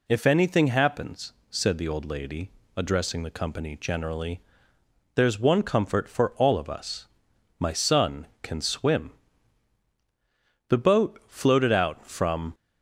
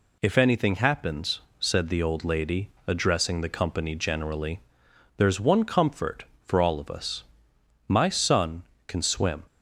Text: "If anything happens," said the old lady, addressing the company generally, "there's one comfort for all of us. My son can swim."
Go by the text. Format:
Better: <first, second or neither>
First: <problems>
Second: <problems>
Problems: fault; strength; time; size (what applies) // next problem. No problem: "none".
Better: second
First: goes on to say "The boat floated out from"; strong; from 10.6 s on; 1.8 s long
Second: none